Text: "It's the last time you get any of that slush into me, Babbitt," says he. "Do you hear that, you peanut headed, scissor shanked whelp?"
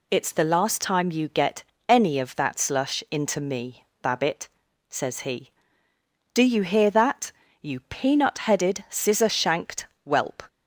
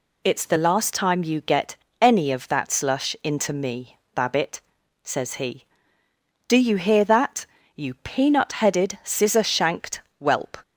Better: neither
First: pauses between "get" and "any"; slight; at 1.6 s; 0.24 s long // pauses between "shanked" and "whelp"; slight; at 9.8 s; 0.18 s long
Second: pauses between "get" and "any"; slight; at 1.7 s; 0.24 s long // pauses between "shanked" and "whelp"; slight; at 10.0 s; 0.18 s long

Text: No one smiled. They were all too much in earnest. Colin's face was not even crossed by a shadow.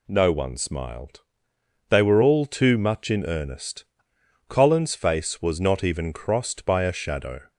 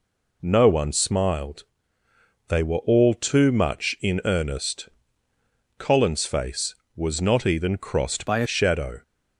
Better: first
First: none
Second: changes voice from "by" to "a"; from 8.2 to 8.4 s; 0.2 s long

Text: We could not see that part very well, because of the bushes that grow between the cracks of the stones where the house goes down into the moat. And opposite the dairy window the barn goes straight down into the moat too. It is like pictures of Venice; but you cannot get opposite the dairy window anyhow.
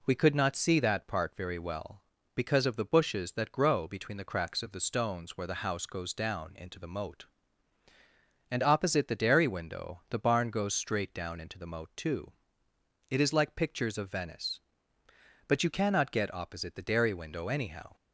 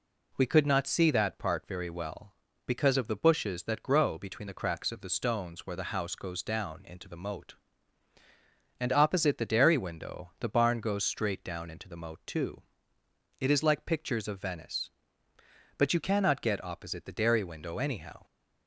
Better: neither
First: none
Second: none

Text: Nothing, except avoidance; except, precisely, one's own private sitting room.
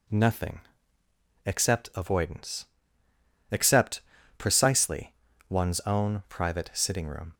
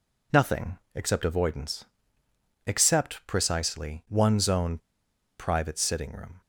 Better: first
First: none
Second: pauses between "own" and "private"; noticeable; at 4.7 s; 0.61 s long

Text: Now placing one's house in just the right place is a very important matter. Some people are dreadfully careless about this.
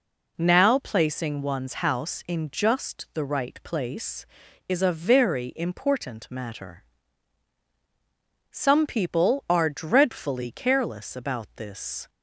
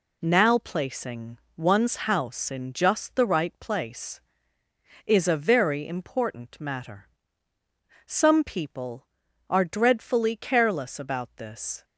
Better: first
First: none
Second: gets quieter; throughout; 6.5 dB // pauses between "placing" and "one's"; slight; at 1.3 s; 0.22 s long

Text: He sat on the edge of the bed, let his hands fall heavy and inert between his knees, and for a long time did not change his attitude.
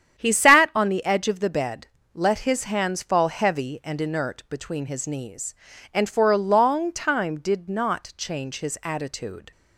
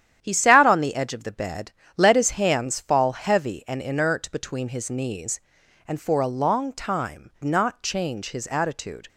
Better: first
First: starts louder than the rest; strong; until 1.2 s; 9 dB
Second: starts louder than the rest; strong; until 1.2 s; 10 dB // skips "did"; at 7.3 s

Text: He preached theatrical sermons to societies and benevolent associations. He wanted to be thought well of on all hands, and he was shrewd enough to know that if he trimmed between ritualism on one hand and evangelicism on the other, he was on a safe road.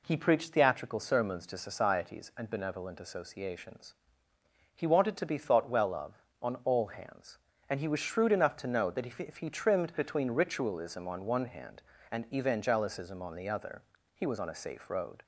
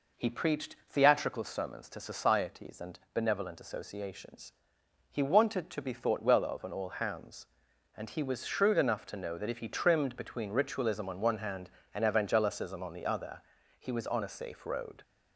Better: second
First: says "if" twice; at 9.1 s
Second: none

